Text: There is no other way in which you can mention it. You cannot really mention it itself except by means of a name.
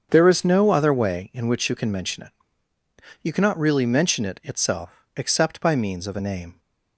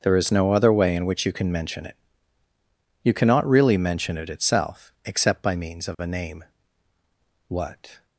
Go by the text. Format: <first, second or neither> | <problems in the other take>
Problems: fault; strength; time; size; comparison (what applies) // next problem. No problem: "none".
first | starts louder than the rest; until 1.0 s; 6.5 dB; strong in the first // goes on to say "What"; from 7.4 s on; 0.58 s long